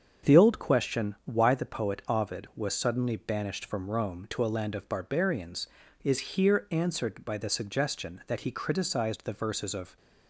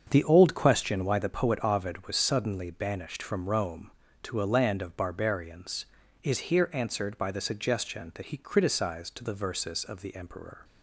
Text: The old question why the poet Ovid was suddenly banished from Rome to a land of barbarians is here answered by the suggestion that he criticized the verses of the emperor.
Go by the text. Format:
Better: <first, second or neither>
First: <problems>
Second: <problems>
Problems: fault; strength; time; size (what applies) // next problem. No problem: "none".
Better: second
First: starts louder than the rest; until 1.3 s; 7 dB // stops before "the emperor"; at 9.9 s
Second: starts louder than the rest; until 1.1 s; 7 dB